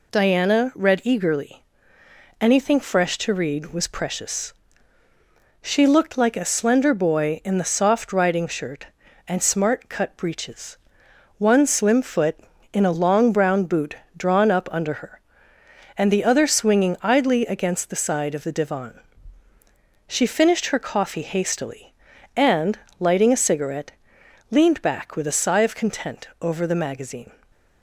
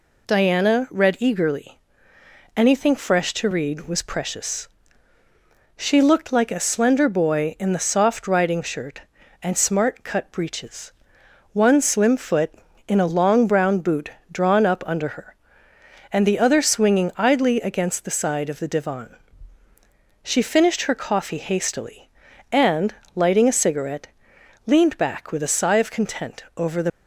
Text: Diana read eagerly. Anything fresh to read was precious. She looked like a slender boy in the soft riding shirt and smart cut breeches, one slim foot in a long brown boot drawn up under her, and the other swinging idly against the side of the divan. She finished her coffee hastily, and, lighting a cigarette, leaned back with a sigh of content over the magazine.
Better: first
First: pauses between "boot" and "drawn"; slight; at 13.9 s; 0.22 s long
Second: pauses between "boot" and "drawn"; slight; at 14.0 s; 0.22 s long // stops before "magazine"; at 26.8 s

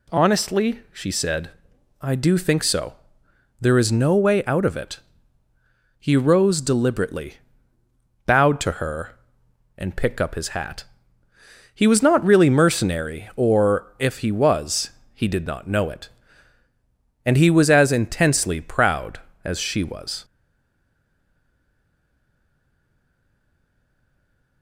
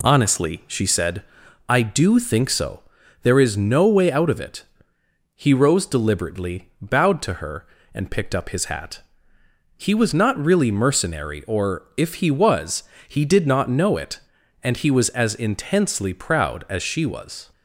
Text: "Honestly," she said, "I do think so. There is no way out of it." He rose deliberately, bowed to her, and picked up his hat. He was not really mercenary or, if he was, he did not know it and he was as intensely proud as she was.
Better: second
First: stays silent after the last word; strong; from 20.2 s on; 4.4 s long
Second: none

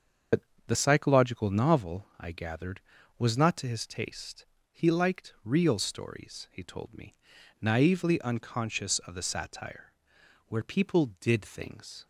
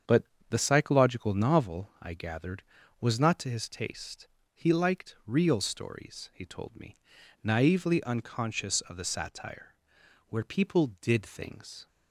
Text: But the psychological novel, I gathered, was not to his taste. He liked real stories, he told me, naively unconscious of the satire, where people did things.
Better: second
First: loses the start of "But"; at 0.3 s; 80 ms // starts louder than the rest; until 1.5 s; 6.5 dB // pauses between "But" and "the"; slight; at 0.4 s; 0.26 s long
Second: starts louder than the rest; strong; until 1.3 s; 7.5 dB // pauses between "But" and "the"; slight; at 0.2 s; 0.26 s long

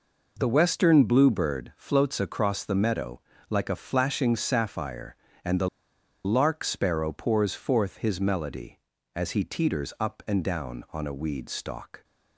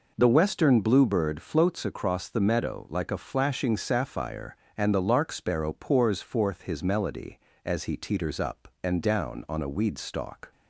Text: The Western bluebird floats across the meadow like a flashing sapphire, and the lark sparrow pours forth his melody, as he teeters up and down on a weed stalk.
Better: second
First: pauses between "meadow" and "like"; slight; at 3.2 s; 0.28 s long // pauses between "the" and "lark"; noticeable; at 5.6 s; 0.56 s long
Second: none

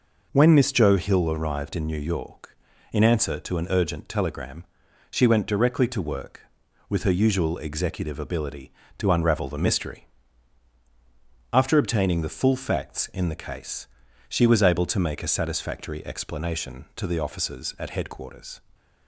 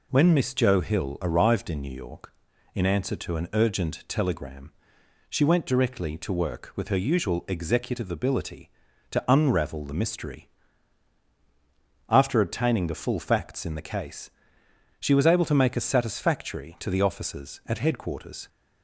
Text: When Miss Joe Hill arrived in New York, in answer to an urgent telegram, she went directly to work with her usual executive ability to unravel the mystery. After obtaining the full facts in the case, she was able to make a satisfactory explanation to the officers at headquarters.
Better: first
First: none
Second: skips "explanation"; at 16.7 s

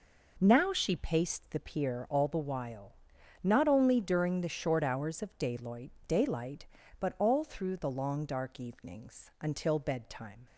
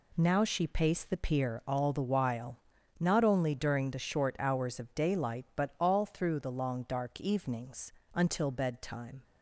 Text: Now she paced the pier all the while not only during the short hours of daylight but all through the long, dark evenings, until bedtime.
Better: second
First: pauses between "while" and "not"; noticeable; at 2.9 s; 0.50 s long // says "daylight" twice; at 6.0 s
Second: pauses between "while" and "not"; at 2.5 s; 0.40 s long

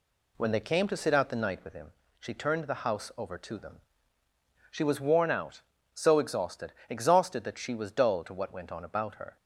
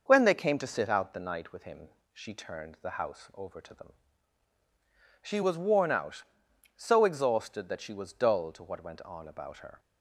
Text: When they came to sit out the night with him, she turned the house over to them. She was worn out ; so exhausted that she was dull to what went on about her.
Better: second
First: says "exhausted" twice; at 6.8 s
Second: none

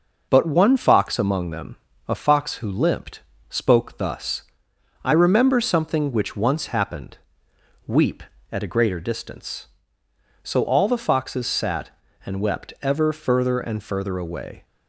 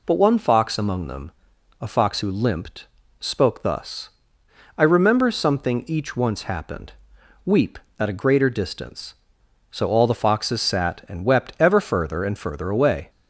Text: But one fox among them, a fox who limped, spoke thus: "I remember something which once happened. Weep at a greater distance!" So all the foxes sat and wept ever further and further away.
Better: first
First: none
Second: says "each" for "which"; at 5.8 s

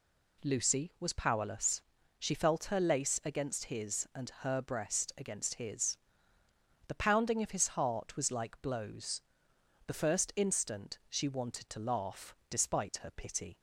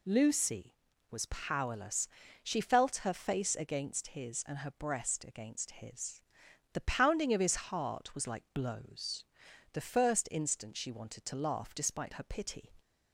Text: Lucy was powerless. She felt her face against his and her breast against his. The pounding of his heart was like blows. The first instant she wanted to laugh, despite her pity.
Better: second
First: says "lace" for "face"; at 2.7 s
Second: none

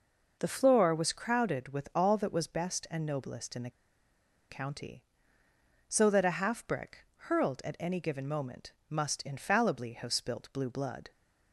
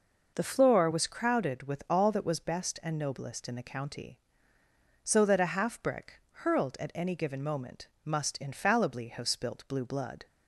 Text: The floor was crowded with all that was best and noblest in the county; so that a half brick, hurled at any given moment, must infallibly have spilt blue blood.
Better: second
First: pauses between "the" and "county"; noticeable; at 3.6 s; 0.79 s long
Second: none

